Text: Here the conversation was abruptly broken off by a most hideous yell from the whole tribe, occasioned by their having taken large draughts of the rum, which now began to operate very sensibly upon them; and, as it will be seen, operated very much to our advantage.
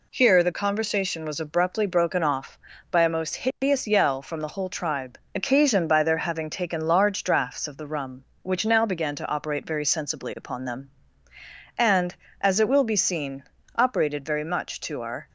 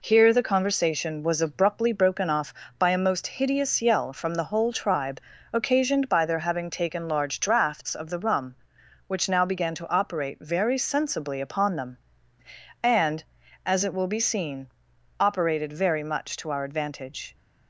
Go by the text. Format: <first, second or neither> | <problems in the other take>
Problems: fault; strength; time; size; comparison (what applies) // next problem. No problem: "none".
second | stops before "advantage"; at 15.2 s